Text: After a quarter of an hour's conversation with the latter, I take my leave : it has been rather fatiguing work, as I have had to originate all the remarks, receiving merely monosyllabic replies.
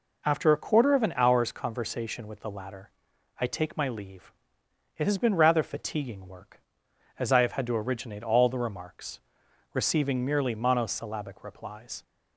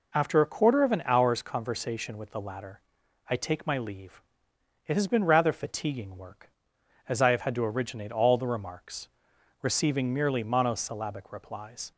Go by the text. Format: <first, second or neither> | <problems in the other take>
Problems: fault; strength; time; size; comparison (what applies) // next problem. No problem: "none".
neither | none